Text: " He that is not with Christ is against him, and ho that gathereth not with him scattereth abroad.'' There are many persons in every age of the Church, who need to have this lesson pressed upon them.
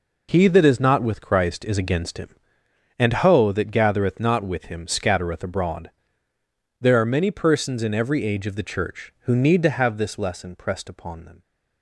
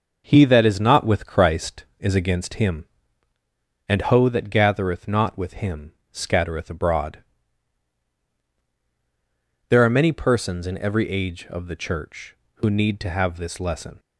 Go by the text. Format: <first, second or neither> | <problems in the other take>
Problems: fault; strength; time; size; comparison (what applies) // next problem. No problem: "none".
first | pauses between "him" and "scattereth"; slight; at 5.9 s; 0.18 s long // stops before "pressed upon them"; at 13.9 s